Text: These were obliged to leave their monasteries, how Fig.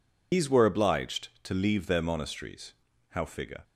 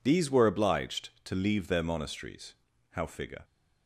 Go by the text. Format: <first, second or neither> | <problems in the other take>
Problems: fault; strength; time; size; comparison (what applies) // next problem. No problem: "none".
second | loses the start of "These"; at 0.3 s; 110 ms